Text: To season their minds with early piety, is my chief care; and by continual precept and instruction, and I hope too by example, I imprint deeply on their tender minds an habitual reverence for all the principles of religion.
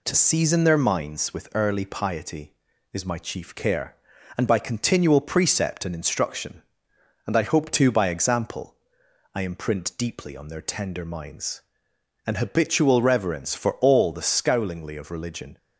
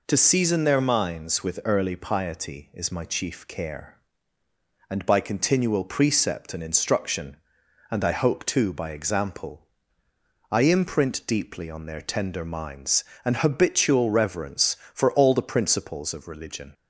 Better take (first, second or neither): second